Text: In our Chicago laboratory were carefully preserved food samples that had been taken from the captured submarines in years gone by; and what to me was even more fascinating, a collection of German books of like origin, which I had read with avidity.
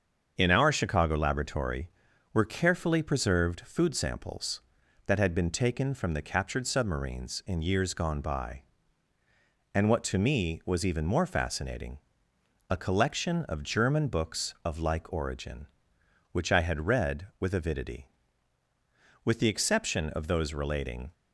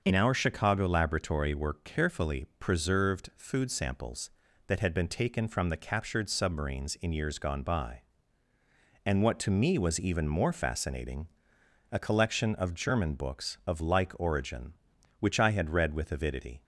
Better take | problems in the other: second | starts louder than the rest; until 1.3 s; 7 dB; also in the second // goes on to say "With the exception of those relating"; strong; from 19.2 s on; 1.9 s long

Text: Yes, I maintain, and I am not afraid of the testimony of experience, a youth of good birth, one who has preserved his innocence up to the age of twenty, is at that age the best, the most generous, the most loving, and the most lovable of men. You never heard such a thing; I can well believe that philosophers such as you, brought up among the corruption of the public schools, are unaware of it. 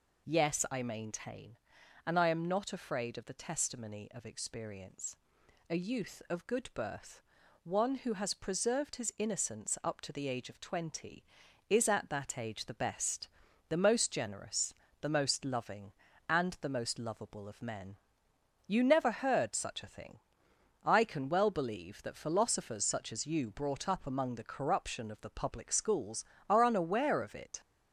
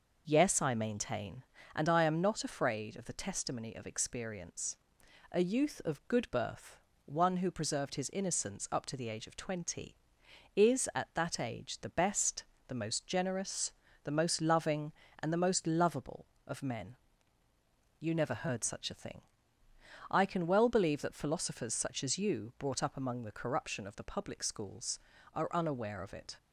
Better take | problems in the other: first | skips "has"; at 7.5 s

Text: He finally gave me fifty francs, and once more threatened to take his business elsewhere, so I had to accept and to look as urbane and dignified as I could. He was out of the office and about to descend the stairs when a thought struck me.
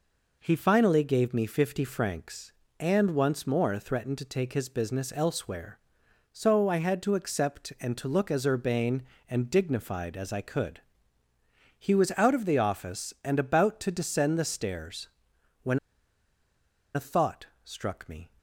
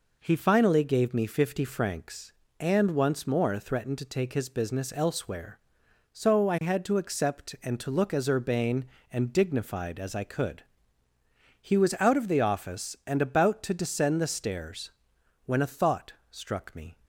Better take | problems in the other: second | pauses between "stairs" and "when"; noticeable; at 15.0 s; 0.54 s long; noticeable in the second // pauses between "when" and "a"; at 15.7 s; 1.1 s long // pauses between "thought" and "struck"; slight; at 17.4 s; 0.18 s long; slight in the second

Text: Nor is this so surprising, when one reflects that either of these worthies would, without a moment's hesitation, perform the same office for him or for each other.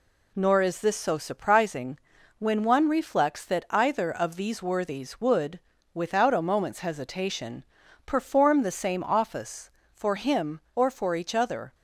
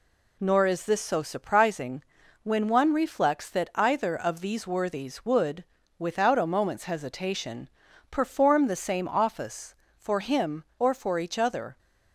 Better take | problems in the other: neither | none

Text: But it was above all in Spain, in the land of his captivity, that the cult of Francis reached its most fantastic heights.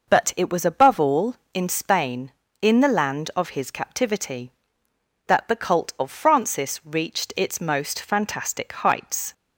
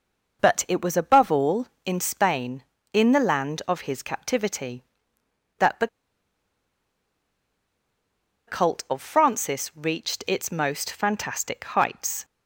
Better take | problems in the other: first | pauses between "the" and "cult"; strong; at 5.8 s; 2.6 s long

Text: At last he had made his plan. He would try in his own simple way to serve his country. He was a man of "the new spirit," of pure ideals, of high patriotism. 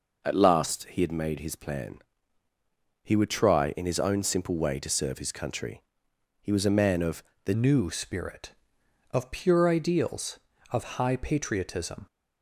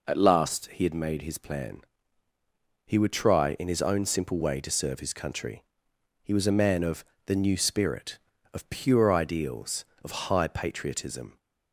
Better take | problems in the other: second | pauses between "of" and "the"; slight; at 7.2 s; 0.22 s long; slight in the second // changes voice at "new"; from 7.5 s on; 4.5 s long

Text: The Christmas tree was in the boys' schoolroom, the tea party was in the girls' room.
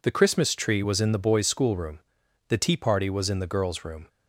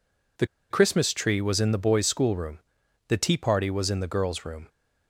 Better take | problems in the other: first | pauses between "The" and "Christmas"; slight; at 0.4 s; 0.24 s long

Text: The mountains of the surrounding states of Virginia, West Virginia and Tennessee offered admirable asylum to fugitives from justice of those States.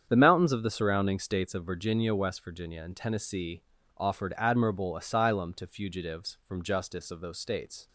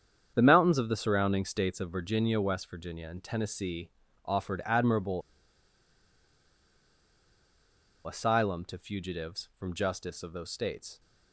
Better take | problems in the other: first | starts louder than the rest; strong; until 1.3 s; 8 dB; strong in the first // pauses between "Tennessee" and "offered"; slight; at 3.9 s; 0.34 s long; slight in the first // pauses between "admirable" and "asylum"; strong; at 5.2 s; 2.8 s long

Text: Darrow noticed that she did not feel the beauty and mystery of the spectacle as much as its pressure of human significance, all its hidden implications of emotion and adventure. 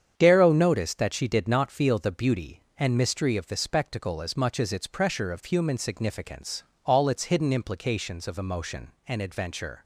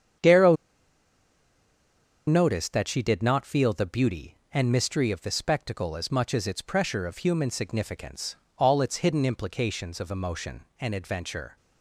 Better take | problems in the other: first | starts louder than the rest; strong; until 2.9 s; 8 dB; strong in the first // pauses between "Darrow" and "noticed"; strong; at 0.5 s; 1.7 s long

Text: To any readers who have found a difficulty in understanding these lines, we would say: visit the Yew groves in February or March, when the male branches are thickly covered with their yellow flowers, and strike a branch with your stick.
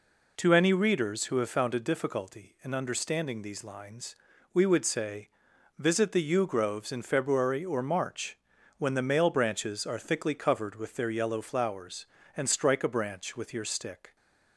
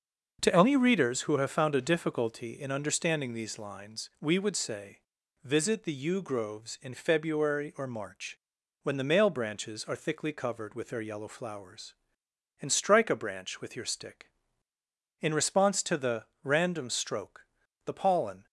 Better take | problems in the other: first | starts louder than the rest; noticeable; until 1.4 s; 6 dB // goes on to say "In response to the random stroke the pollen"; strong; from 15.1 s on; 3.2 s long

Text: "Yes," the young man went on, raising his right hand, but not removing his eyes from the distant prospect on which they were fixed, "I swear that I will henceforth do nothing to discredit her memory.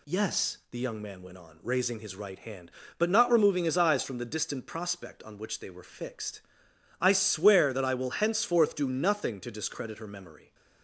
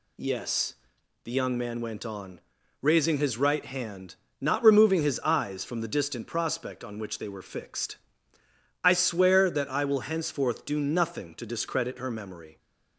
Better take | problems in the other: first | skips "but"; at 4.2 s

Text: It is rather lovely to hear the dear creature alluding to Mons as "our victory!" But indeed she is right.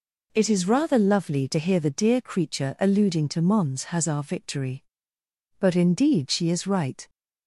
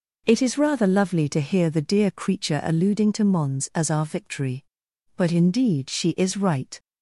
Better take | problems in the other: second | says "has" for "as"; at 3.8 s

